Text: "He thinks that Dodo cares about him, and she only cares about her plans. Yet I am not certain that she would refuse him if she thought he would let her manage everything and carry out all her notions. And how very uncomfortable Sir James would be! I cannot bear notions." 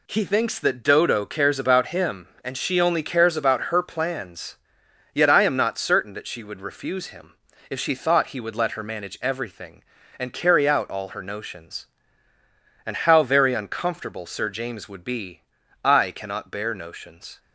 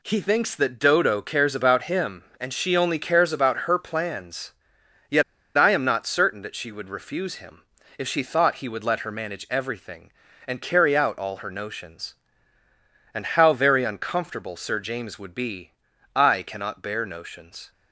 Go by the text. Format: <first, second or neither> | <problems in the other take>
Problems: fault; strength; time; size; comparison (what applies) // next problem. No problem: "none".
first | pauses between "Yet" and "I"; slight; at 5.2 s; 0.33 s long // pauses between "him" and "if"; slight; at 7.6 s; 0.36 s long; slight in the first